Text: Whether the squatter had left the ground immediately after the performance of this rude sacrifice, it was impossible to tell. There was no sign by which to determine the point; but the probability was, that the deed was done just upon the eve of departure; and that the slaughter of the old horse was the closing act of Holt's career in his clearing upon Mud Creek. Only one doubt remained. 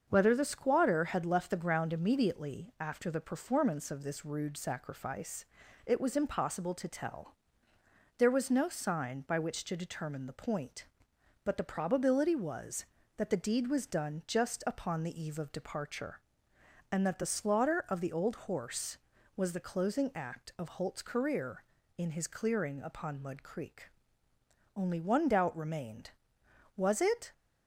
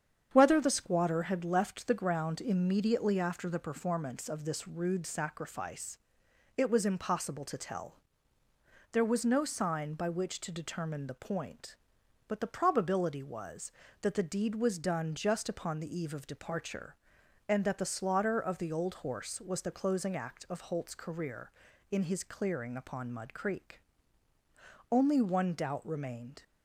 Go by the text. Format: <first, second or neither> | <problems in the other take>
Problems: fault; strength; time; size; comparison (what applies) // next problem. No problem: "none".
second | starts louder than the rest; until 1.0 s; 6.5 dB; strong in the second // goes on to say "Was it"; from 26.7 s on; 0.56 s long